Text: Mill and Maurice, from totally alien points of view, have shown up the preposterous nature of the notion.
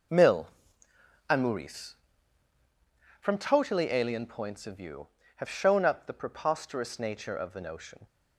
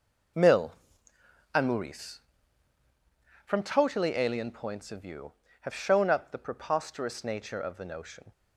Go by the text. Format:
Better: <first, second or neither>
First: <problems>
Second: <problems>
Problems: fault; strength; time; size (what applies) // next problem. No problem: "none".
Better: neither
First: none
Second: none